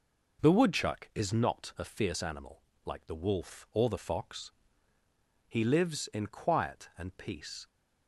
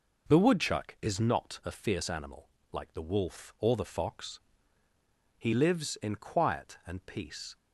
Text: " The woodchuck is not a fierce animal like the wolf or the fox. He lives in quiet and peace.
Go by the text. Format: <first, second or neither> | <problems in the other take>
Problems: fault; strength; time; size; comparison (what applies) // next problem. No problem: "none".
neither | pauses between "animal" and "like"; slight; the same in both